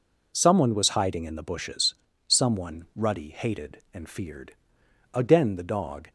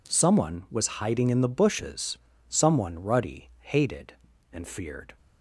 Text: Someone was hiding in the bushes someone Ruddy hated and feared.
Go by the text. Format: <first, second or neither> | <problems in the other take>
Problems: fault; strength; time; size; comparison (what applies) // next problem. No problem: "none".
second | pauses between "bushes" and "someone"; slight; at 1.9 s; 0.32 s long; slight in the second // goes on to say "Again the dog"; noticeable; from 5.1 s on; 0.96 s long